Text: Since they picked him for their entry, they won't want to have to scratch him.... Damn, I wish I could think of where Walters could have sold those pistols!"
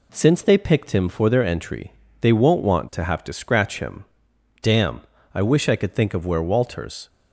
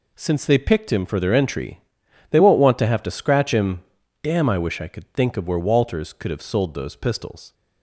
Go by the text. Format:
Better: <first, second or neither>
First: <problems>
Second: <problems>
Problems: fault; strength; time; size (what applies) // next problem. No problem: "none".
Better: second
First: stops before "could have sold those pistols"; at 7.0 s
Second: none